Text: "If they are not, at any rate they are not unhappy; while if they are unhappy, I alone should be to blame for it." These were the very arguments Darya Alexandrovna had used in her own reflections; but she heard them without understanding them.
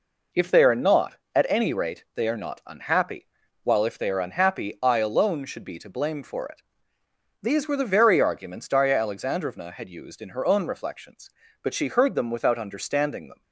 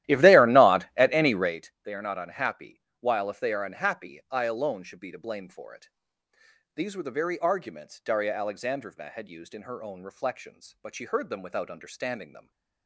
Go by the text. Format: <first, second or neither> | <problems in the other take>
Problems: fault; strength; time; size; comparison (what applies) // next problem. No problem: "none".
first | starts louder than the rest; strong; until 1.6 s; 14.5 dB